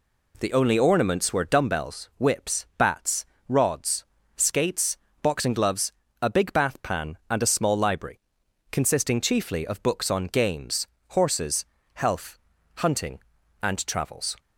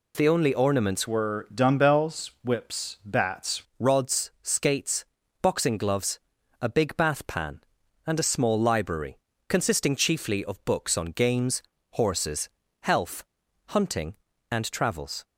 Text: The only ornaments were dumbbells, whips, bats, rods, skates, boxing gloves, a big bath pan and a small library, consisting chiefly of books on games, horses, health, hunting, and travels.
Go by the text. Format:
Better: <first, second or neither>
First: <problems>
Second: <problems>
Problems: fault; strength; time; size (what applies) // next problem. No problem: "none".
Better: first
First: none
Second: changes voice from "were" to "bats"; from 1.0 to 3.6 s; 2.6 s long